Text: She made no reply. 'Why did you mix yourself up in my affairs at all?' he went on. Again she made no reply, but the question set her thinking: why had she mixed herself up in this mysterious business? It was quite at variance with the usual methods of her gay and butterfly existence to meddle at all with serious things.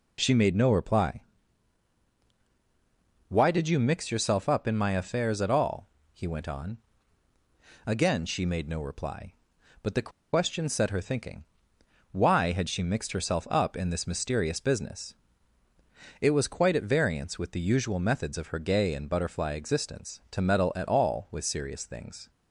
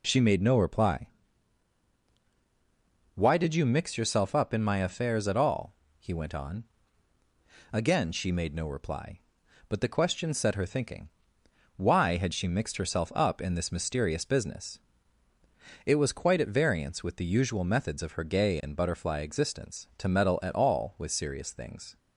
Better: second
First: pauses between "the" and "question"; slight; at 10.0 s; 0.23 s long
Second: none

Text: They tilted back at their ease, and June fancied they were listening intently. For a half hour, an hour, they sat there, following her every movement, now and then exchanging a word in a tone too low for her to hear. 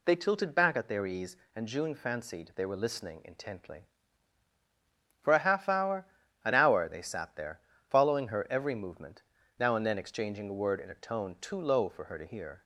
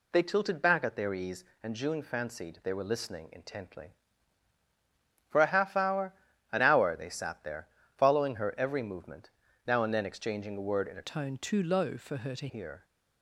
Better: first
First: none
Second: changes voice from "tone" to "to"; from 11.0 to 12.4 s; 1.4 s long

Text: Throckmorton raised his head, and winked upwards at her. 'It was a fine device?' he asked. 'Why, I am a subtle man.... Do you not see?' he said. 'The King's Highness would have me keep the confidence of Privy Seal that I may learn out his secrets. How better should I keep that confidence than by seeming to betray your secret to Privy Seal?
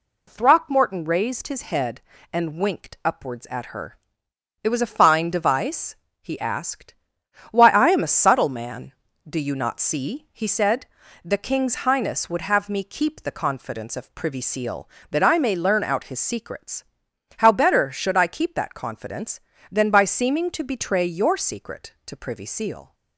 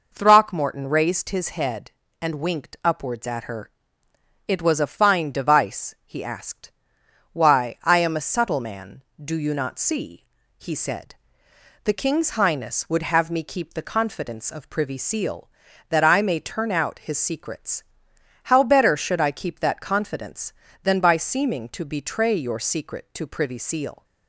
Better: first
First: none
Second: says "turn" for "learn"; at 16.3 s

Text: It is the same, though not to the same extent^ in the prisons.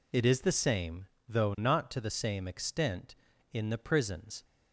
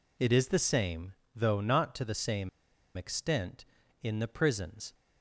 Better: first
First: none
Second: pauses between "same" and "extent"; noticeable; at 2.4 s; 0.48 s long

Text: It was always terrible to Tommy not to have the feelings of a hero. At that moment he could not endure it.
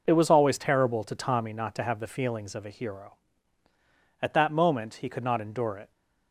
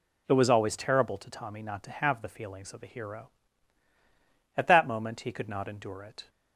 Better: neither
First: none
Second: none

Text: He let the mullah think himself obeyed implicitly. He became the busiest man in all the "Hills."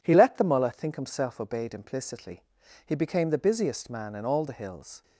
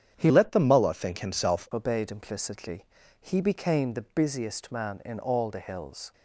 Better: first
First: none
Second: starts louder than the rest; strong; until 1.1 s; 9 dB // changes voice from "let" to "himself"; from 0.2 to 1.6 s; 1.4 s long

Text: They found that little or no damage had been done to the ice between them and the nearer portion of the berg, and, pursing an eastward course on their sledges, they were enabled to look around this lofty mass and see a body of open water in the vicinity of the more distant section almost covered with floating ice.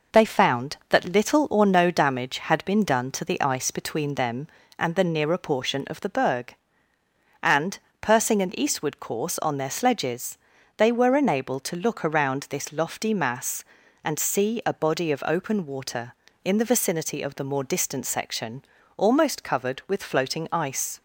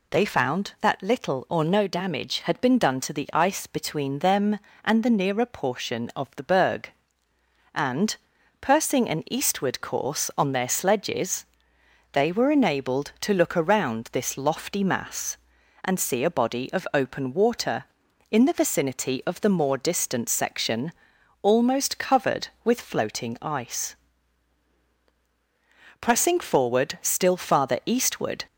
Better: first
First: pauses between "section" and "almost"; slight; at 18.6 s; 0.32 s long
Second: pauses between "section" and "almost"; noticeable; at 20.9 s; 0.50 s long // goes on to say "Pressing forward still farther eastward"; strong; from 26.0 s on; 2.4 s long

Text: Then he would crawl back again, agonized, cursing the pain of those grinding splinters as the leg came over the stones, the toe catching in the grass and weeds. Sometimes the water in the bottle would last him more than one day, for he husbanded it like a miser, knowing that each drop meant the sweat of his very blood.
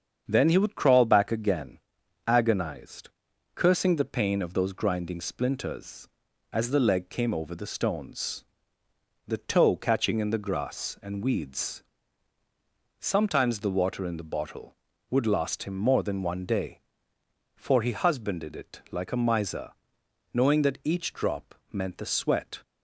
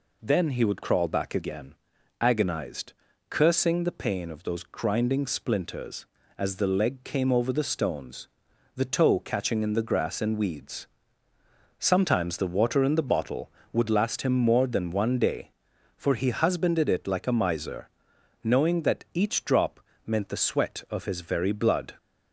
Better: second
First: starts louder than the rest; strong; until 1.3 s; 7.5 dB // pauses between "drop" and "meant"; slight; at 21.5 s; 0.18 s long // stops before "of his very blood"; at 22.6 s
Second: pauses between "drop" and "meant"; slight; at 19.8 s; 0.26 s long

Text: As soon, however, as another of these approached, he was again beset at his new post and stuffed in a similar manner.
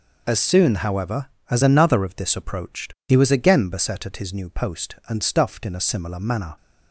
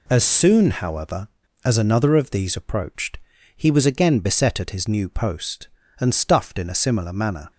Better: second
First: says "this" for "these"; at 2.1 s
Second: none

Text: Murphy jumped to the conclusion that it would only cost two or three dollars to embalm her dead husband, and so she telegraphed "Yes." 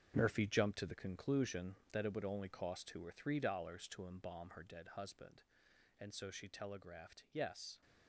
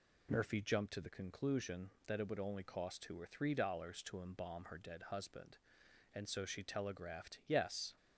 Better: second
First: gets quieter; strong; throughout; 10 dB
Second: none

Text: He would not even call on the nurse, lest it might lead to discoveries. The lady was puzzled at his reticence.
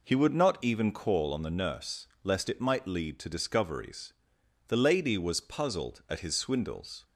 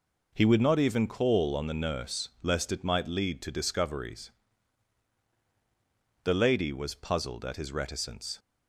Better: second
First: says "swindles" for "reticence"; at 6.3 s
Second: none

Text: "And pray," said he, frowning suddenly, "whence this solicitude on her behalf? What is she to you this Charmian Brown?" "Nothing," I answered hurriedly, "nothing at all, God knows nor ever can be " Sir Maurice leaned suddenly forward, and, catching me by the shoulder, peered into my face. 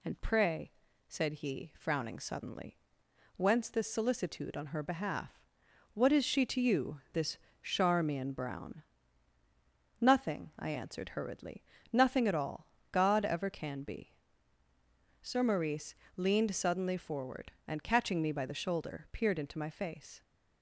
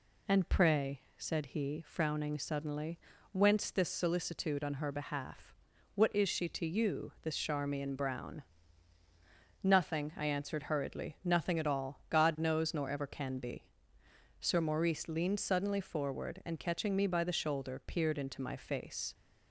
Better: second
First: pauses between "this" and "Charmian"; slight; at 7.3 s; 0.24 s long // skips "knows nor"; at 13.2 s // pauses between "Maurice" and "leaned"; slight; at 15.9 s; 0.24 s long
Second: none

